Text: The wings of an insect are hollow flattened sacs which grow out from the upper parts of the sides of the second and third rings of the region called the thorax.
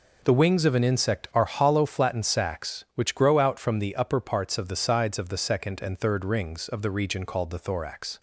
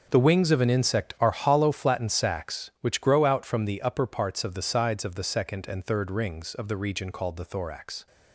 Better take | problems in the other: first | gets quieter; strong; throughout; 13 dB

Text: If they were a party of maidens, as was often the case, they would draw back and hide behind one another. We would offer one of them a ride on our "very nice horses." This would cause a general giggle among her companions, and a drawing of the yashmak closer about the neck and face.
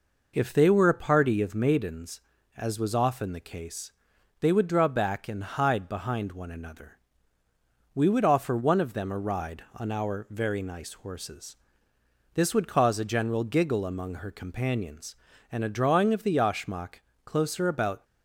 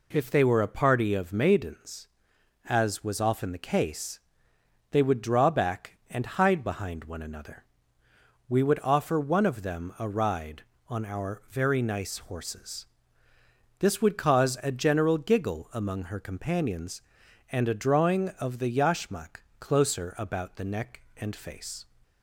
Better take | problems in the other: second | pauses between "yashmak" and "closer"; slight; at 17.0 s; 0.24 s long // stops before "the neck and face"; at 18.0 s

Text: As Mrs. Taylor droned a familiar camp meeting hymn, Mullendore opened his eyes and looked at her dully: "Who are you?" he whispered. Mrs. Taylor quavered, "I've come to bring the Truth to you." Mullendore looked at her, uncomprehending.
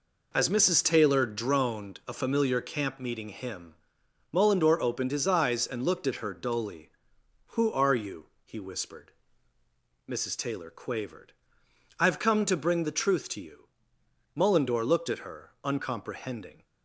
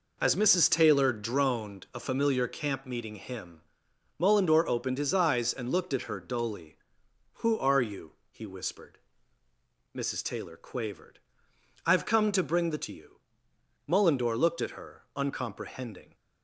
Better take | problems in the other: first | skips "Truth"; at 12.8 s

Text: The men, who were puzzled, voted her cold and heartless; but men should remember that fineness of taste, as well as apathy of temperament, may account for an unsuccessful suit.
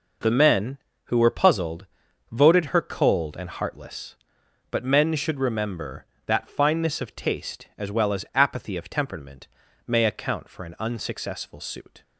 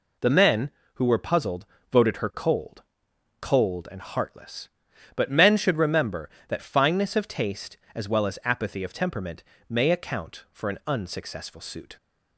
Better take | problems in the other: first | says "cold" twice; at 3.4 s

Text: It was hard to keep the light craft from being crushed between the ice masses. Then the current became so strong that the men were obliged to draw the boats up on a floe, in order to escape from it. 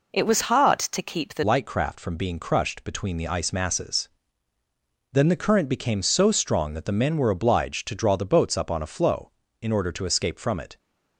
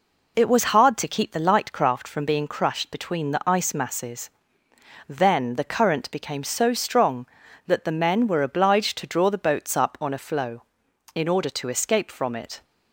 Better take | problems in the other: second | changes voice at "light"; from 1.4 s on; 9.3 s long

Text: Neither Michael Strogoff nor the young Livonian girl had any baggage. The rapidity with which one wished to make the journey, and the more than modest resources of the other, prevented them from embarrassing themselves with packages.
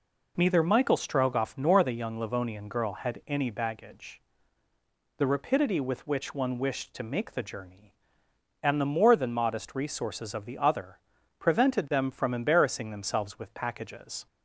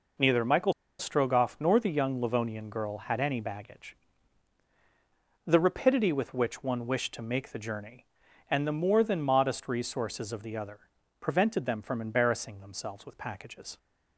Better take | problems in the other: first | pauses between "Michael" and "Strogoff"; slight; at 0.7 s; 0.26 s long

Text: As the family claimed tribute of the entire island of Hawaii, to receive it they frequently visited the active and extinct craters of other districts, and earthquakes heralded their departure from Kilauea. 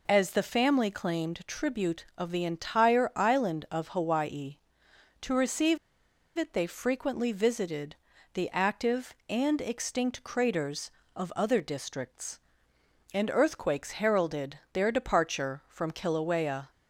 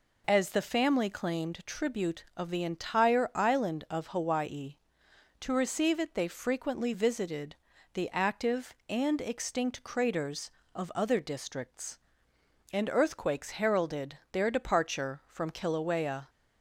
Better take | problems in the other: second | pauses between "receive" and "it"; noticeable; at 5.7 s; 0.60 s long // pauses between "visited" and "the"; slight; at 7.9 s; 0.36 s long; slight in the second

